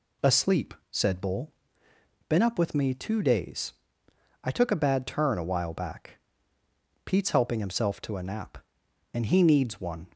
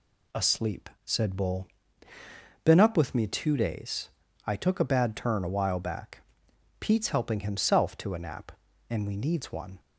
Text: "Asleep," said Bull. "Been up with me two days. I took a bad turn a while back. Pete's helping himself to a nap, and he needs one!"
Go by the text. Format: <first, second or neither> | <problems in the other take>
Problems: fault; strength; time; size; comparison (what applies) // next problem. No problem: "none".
first | says "we" for "he"; at 9.0 s